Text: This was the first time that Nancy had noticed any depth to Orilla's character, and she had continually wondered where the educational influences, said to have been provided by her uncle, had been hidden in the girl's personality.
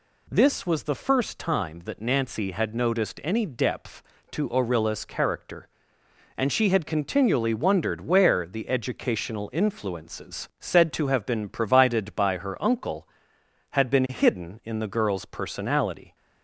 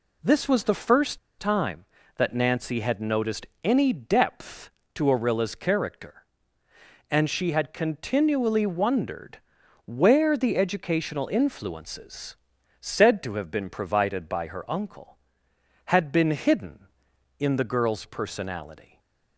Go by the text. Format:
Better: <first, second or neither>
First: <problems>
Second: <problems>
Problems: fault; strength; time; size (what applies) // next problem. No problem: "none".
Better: first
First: none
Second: pauses between "first" and "time"; slight; at 1.1 s; 0.20 s long // pauses between "noticed" and "any"; slight; at 3.4 s; 0.16 s long // pauses between "wondered" and "where"; noticeable; at 9.3 s; 0.46 s long // stays silent after the last word; slight; from 18.8 s on; 0.5 s long